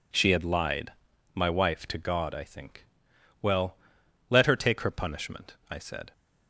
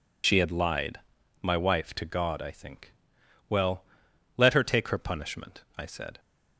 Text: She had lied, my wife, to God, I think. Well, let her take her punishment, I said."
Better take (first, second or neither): first